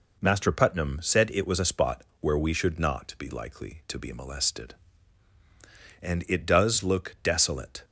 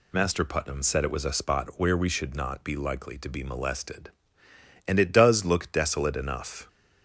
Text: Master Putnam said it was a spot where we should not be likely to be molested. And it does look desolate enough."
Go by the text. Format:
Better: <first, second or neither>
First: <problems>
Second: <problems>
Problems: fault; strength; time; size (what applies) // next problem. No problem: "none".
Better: second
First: pauses between "spot" and "where"; slight; at 2.0 s; 0.18 s long // stops before "enough"; at 7.8 s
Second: none